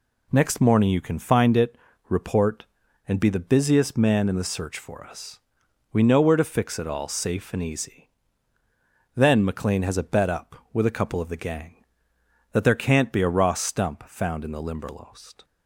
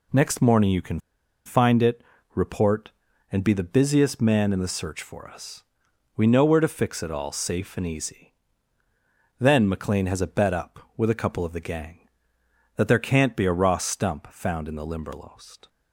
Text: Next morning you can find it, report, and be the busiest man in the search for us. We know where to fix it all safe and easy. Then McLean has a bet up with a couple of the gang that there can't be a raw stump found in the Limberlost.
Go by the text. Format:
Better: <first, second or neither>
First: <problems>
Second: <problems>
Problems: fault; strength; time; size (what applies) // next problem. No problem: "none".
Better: first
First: none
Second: pauses between "can" and "find"; noticeable; at 0.9 s; 0.46 s long